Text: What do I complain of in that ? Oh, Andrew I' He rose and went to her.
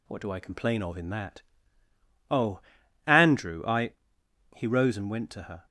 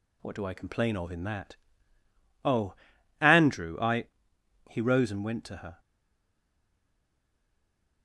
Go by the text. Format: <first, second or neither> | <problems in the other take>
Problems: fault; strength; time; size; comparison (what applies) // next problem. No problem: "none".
first | pauses between "I" and "He"; noticeable; at 4.0 s; 0.60 s long; noticeable in the first // stays silent after the last word; from 5.7 s on; 2.3 s long